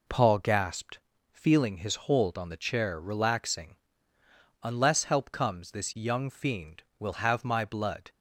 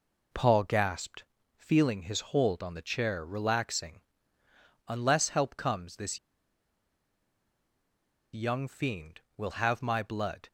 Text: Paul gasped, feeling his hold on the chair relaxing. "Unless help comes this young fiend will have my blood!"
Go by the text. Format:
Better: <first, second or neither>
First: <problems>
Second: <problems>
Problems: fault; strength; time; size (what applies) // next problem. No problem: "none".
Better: first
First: none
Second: pauses between "this" and "young"; strong; at 6.1 s; 2.1 s long